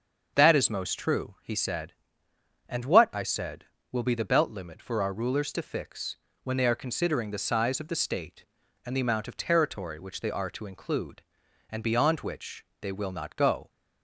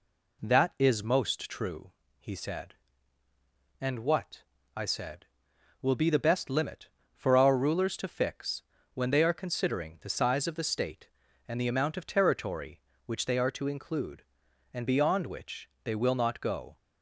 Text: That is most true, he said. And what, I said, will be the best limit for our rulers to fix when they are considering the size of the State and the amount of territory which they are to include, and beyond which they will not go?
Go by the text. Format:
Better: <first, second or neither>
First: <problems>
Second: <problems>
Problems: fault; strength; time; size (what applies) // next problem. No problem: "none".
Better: second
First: starts louder than the rest; until 1.3 s; 6.5 dB // says "belt" for "best"; at 4.2 s // pauses between "fix" and "when"; slight; at 6.1 s; 0.28 s long // pauses between "which" and "they"; slight; at 12.6 s; 0.16 s long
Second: pauses between "fix" and "when"; slight; at 8.6 s; 0.32 s long // pauses between "which" and "they"; slight; at 15.6 s; 0.16 s long